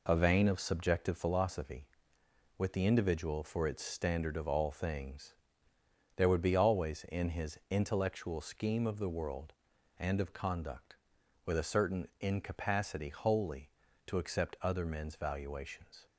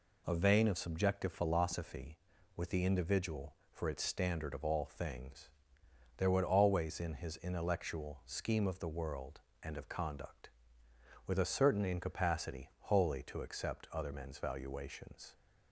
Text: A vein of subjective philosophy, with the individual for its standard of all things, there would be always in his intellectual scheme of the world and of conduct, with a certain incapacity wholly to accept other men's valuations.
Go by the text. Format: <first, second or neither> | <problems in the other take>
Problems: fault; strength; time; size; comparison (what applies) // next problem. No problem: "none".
first | skips "be"; at 6.4 s